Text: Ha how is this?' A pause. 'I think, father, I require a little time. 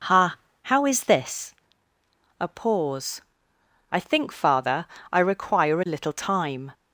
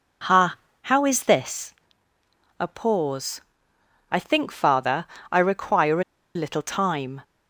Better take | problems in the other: first | pauses between "Ha" and "how"; slight; at 0.5 s; 0.28 s long; slight in the first // pauses between "a" and "little"; slight; at 6.0 s; 0.32 s long

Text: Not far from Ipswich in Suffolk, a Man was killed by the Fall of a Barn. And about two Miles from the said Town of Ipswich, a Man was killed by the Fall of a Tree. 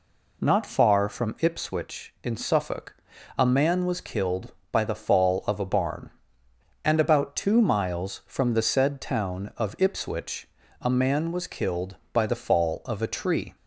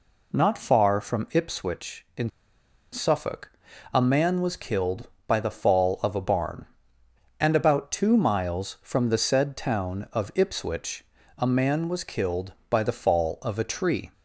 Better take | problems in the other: first | pauses between "in" and "Suffolk"; noticeable; at 2.2 s; 0.62 s long

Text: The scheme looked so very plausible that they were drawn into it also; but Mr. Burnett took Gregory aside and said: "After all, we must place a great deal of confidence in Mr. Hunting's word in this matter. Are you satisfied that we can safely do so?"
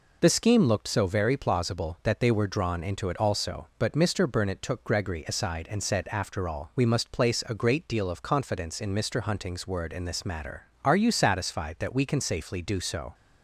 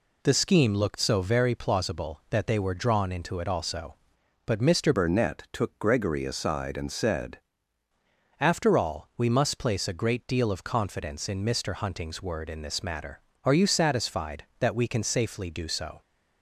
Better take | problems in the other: first | changes voice from "Burnett" to "said"; from 4.9 to 7.3 s; 2.4 s long

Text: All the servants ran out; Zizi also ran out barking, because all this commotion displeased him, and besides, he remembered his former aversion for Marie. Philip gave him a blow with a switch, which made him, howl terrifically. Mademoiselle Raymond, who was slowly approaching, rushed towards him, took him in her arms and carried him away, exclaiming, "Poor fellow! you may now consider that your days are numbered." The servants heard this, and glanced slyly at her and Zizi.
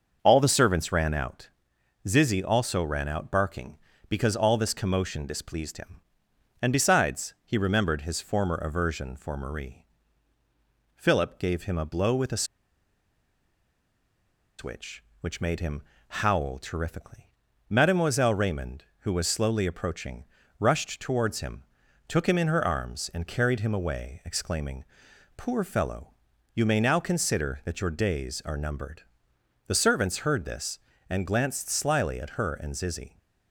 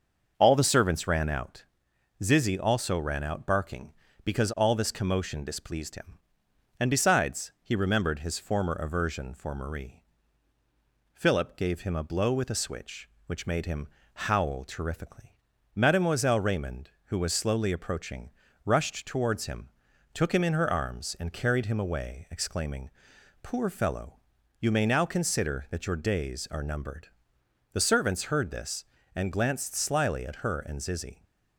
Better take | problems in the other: second | starts louder than the rest; until 1.2 s; 6.5 dB; also in the second // pauses between "a" and "switch"; strong; at 12.4 s; 2.1 s long

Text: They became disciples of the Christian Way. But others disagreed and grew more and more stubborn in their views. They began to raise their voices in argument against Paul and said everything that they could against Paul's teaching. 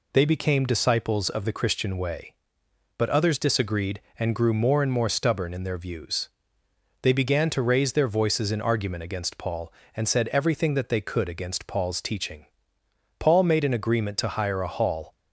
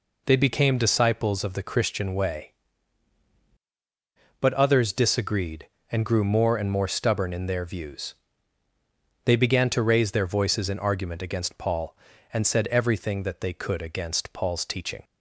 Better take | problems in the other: second | goes on to say "Paul made an agreement to hire a hall"; strong; from 13.1 s on; 1.9 s long

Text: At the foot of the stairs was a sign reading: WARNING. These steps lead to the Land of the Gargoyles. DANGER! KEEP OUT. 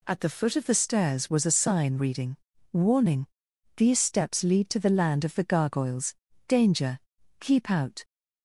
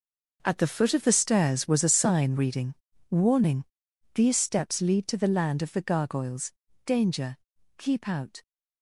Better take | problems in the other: first | gets quieter; strong; throughout; 12 dB

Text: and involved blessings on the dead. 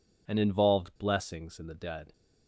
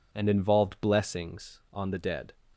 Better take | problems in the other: second | says "in" for "on"; at 1.5 s

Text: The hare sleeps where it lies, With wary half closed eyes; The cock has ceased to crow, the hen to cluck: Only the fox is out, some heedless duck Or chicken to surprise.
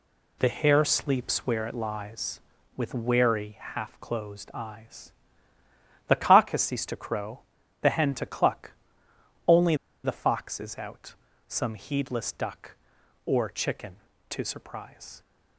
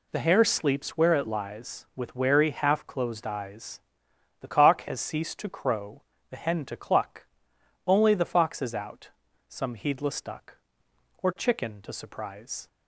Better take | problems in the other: second | pauses between "Only" and "the"; slight; at 9.7 s; 0.29 s long

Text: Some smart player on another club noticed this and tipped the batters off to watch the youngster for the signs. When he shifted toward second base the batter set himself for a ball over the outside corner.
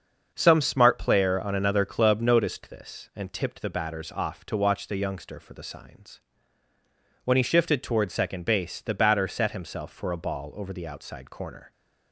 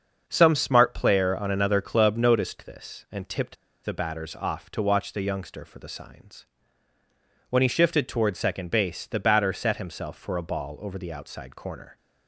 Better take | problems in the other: first | starts louder than the rest; until 1.2 s; 6.5 dB; also in the first // pauses between "tipped" and "the"; slight; at 3.5 s; 0.28 s long

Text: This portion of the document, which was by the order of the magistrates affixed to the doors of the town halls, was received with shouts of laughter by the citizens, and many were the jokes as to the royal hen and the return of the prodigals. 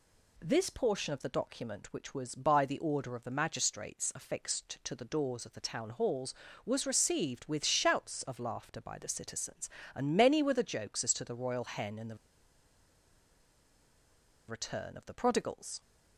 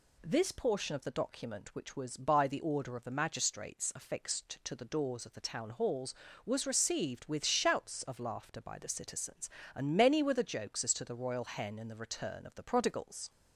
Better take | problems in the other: second | pauses between "the" and "return"; strong; at 12.1 s; 2.3 s long

